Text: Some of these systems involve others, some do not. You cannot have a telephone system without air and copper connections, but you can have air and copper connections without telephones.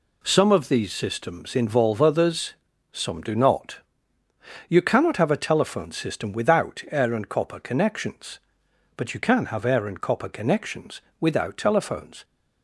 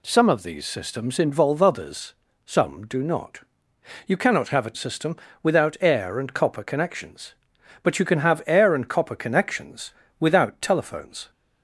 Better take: first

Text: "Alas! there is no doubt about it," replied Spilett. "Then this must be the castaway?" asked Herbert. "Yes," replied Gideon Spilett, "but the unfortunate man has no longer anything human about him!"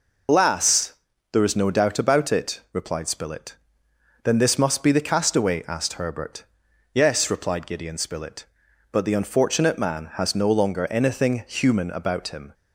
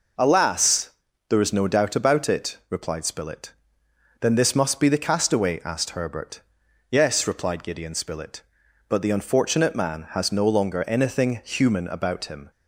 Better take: second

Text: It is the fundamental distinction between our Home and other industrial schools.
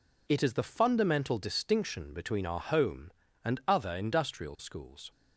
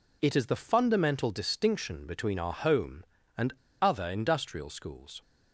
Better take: first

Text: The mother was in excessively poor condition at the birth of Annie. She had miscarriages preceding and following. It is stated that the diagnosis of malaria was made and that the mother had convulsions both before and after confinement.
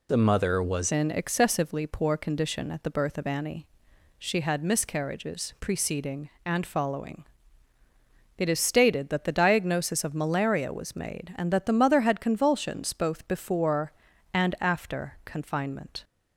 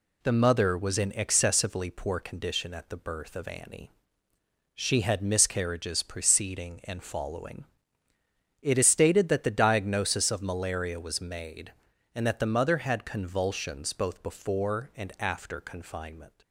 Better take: second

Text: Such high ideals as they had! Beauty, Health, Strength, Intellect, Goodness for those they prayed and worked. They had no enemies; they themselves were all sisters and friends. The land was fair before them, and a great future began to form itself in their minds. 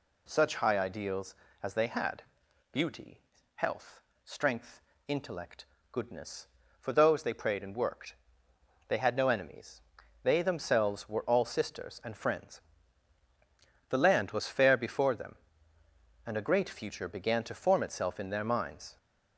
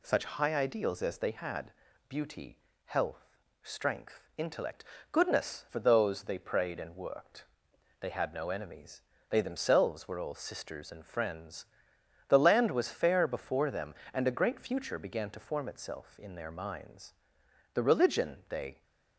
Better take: first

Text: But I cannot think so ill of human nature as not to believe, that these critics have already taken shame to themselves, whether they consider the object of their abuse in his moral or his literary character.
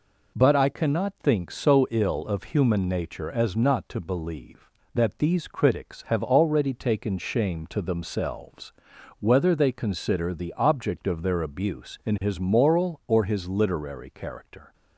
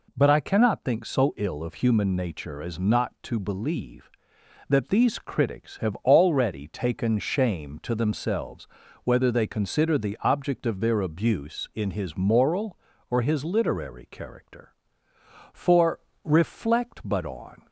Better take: first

